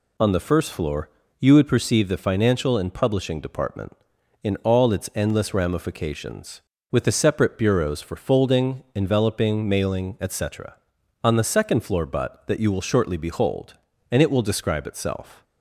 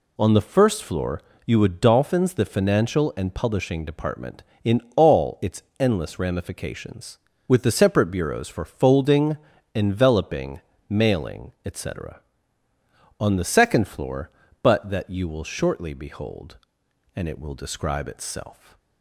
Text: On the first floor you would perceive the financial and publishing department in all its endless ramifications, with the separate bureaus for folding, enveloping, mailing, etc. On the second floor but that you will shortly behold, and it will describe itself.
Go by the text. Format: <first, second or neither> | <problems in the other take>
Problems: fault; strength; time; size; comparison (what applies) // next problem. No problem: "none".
first | pauses between "floor" and "you"; slight; at 1.2 s; 0.26 s long; slight in the first // says "dolphins" for "perceive"; at 1.8 s // pauses between "in" and "all"; slight; at 4.8 s; 0.16 s long // pauses between "its" and "endless"; slight; at 5.6 s; 0.16 s long